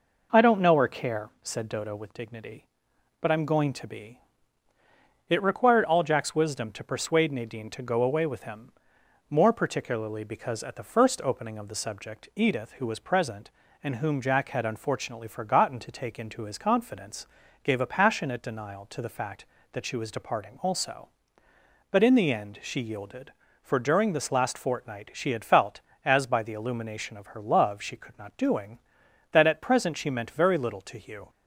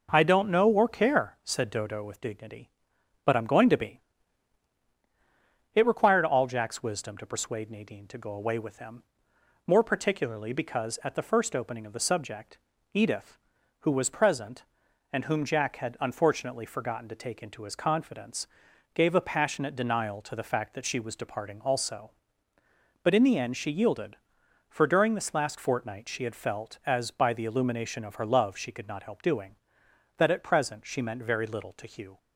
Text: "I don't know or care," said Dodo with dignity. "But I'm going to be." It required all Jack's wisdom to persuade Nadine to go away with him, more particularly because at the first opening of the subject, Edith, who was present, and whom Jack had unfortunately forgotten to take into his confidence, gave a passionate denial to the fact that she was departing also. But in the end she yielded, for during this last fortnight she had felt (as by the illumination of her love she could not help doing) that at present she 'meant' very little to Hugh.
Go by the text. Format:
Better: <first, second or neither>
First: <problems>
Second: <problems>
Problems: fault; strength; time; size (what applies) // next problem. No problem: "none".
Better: second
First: skips "help"; at 28.3 s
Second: none